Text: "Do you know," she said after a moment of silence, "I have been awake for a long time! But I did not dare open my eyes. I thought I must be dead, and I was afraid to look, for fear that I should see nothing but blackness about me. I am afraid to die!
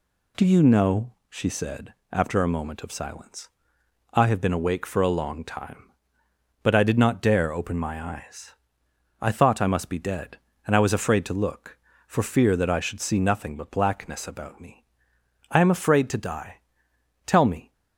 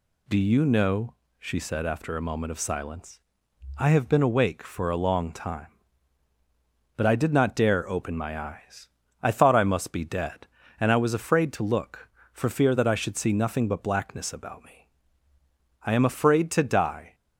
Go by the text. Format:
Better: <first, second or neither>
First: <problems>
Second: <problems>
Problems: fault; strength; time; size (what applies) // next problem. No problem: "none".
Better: second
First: pauses between "said" and "after"; slight; at 1.9 s; 0.18 s long // goes on to say "Tell me"; slight; from 17.2 s on; 0.46 s long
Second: none